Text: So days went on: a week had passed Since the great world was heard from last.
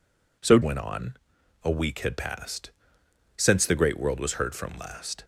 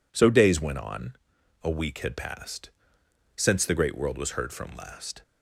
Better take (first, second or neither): second